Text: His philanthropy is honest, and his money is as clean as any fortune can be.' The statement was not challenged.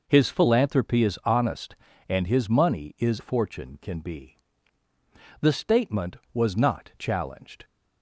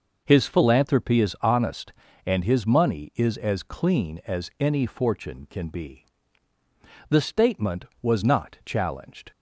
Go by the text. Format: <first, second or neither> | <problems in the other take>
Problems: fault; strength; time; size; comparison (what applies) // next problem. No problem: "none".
second | skips "as clean as any"; at 3.1 s